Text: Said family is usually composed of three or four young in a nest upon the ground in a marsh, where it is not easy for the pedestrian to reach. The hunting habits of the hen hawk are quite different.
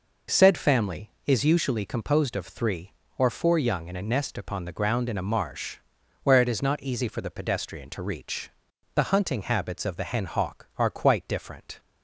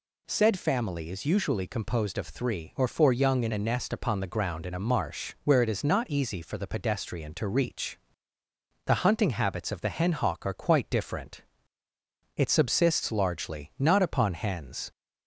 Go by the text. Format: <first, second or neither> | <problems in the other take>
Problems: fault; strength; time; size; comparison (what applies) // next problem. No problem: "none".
first | goes on to say "It subsists largely not upon hens"; strong; from 12.3 s on; 2.5 s long